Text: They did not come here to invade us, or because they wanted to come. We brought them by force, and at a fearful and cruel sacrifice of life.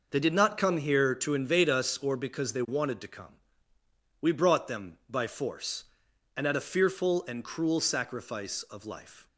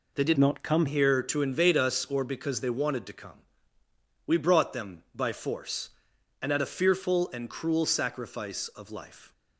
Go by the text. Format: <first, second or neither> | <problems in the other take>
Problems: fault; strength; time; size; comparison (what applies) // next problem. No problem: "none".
first | changes voice from "not" to "come"; from 0.3 to 0.8 s; 0.5 s long